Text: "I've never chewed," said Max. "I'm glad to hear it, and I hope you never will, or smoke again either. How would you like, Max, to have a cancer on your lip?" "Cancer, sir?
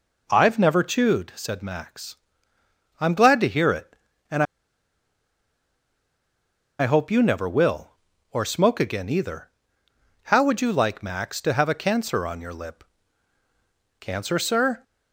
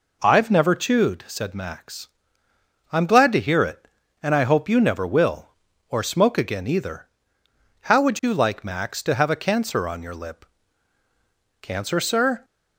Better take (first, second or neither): second